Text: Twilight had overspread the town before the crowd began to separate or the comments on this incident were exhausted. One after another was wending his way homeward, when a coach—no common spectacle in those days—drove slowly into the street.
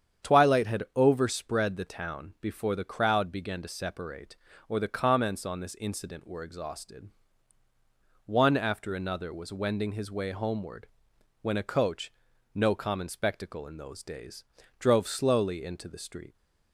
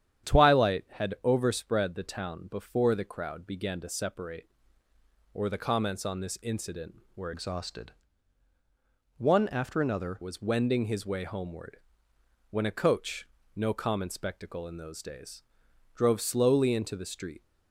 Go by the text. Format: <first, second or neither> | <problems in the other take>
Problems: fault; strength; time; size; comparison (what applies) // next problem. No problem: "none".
first | starts louder than the rest; strong; until 1.3 s; 9.5 dB; strong in the first // changes voice from "exhausted" to "another"; from 7.3 to 10.2 s; 2.9 s long